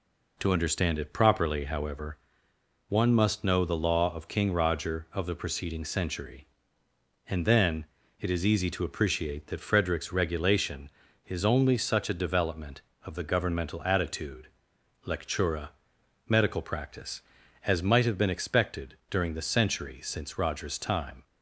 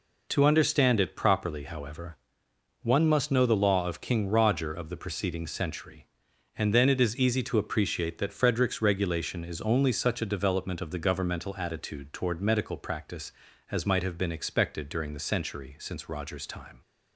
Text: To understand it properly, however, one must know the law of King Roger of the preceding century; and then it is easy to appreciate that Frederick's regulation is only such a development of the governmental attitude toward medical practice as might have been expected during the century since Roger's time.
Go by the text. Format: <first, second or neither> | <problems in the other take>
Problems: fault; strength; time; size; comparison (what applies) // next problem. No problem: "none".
second | pauses between "then" and "it"; slight; at 7.8 s; 0.34 s long // says "lectura" for "toward"; at 15.0 s